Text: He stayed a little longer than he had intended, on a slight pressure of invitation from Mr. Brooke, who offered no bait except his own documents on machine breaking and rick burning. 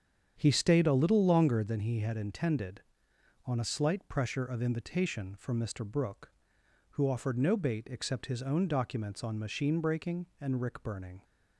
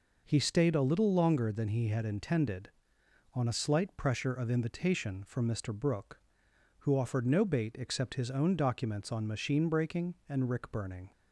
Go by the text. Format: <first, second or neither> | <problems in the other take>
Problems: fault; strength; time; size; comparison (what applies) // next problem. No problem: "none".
second | starts louder than the rest; strong; until 1.8 s; 8 dB